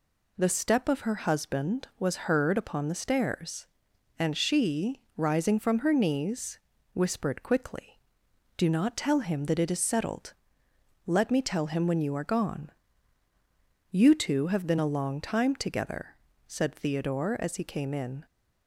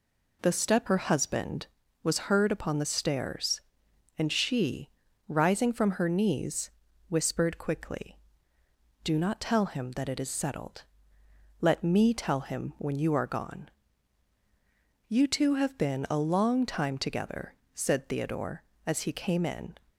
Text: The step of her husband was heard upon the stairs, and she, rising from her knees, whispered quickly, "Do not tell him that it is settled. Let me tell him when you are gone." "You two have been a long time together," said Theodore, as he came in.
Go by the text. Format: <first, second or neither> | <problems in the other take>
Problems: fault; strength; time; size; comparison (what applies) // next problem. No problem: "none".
first | skips "of"; at 0.8 s